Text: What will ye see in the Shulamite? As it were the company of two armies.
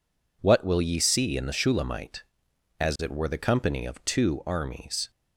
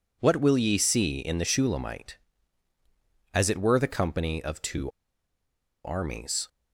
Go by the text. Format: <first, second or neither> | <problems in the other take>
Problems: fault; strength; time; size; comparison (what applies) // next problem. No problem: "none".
first | pauses between "two" and "armies"; noticeable; at 4.9 s; 0.94 s long